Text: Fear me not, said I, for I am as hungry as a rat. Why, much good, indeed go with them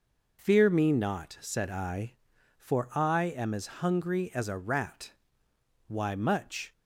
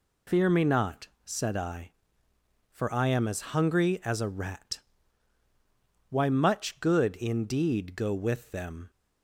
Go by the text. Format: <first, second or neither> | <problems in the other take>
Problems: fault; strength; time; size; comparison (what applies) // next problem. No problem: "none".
second | stops before "good indeed go with them"; at 6.7 s